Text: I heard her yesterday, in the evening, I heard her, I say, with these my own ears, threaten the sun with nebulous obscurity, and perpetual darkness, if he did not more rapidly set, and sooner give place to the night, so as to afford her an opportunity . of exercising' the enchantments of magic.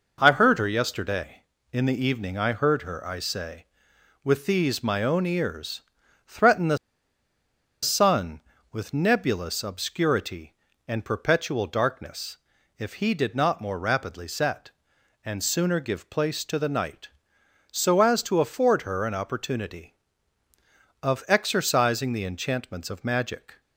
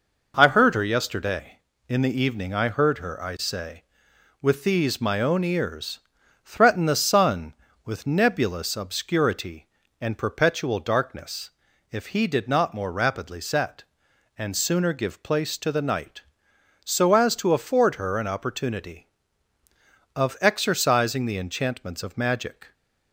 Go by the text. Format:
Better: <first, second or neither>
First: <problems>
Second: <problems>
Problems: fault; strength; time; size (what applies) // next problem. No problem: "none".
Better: second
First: pauses between "the" and "sun"; at 6.7 s; 1.0 s long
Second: none